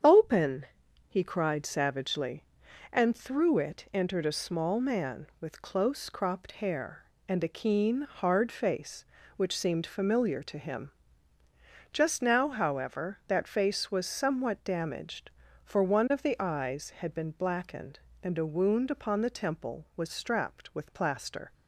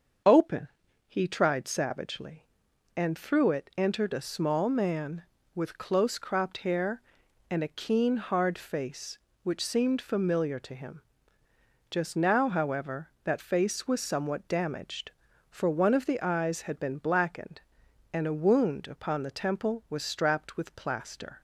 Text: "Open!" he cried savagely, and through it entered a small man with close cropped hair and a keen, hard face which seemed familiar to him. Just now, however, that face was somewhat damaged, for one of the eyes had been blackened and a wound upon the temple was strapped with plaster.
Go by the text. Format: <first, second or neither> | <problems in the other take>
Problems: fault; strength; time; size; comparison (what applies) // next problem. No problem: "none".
first | starts louder than the rest; until 1.6 s; 6.5 dB; strong in the first // says "tried" for "cried"; at 1.2 s